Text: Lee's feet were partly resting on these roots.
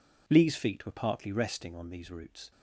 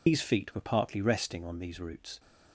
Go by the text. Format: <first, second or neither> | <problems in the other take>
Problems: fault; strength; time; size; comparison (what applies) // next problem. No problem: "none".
first | loses the start of "Lee's"; at 0.0 s; 125 ms